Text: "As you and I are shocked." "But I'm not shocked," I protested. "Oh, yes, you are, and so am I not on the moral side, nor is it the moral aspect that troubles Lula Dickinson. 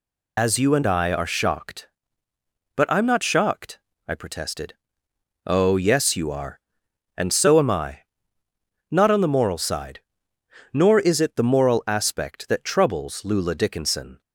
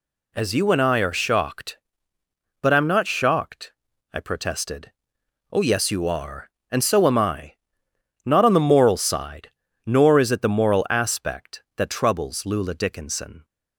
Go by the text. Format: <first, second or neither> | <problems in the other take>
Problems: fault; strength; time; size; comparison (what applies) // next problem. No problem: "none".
second | loses the start of "As"; at 0.3 s; 30 ms // pauses between "I" and "not"; noticeable; at 8.0 s; 0.90 s long; noticeable in the second